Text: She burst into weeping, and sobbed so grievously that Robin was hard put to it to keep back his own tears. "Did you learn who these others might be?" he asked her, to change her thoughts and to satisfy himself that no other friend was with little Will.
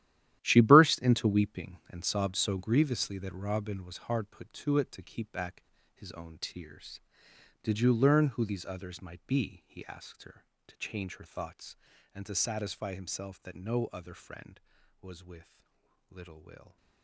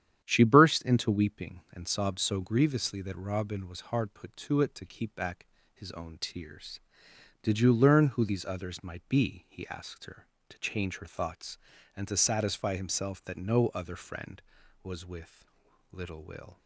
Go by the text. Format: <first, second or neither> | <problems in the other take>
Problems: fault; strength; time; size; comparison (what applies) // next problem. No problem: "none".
second | gets quieter; strong; throughout; 12 dB // starts louder than the rest; strong; until 1.4 s; 12.5 dB; strong in the second // pauses between "back" and "his"; slight; at 5.6 s; 0.31 s long; slight in the second // pauses between "with" and "little"; noticeable; at 15.6 s; 0.48 s long; noticeable in the second